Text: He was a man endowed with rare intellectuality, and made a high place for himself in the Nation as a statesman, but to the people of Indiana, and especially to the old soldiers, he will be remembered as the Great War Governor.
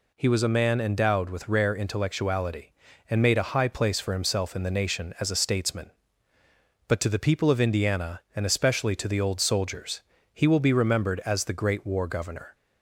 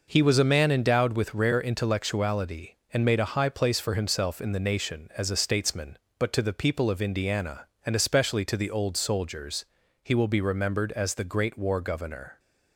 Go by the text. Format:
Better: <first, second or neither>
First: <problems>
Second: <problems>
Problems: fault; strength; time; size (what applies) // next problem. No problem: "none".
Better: neither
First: none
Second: none